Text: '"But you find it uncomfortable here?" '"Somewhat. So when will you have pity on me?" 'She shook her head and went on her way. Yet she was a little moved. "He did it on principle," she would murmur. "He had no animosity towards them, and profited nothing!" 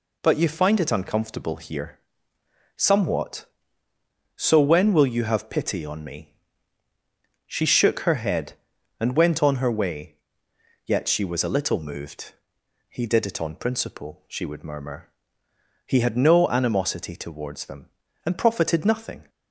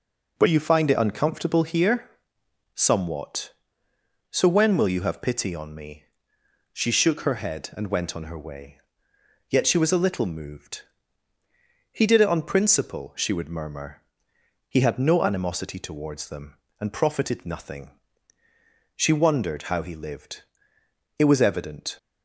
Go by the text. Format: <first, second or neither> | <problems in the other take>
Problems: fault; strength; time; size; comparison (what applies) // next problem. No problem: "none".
first | goes on to say "She wondered how he lived It was evident"; strong; from 18.9 s on; 3.0 s long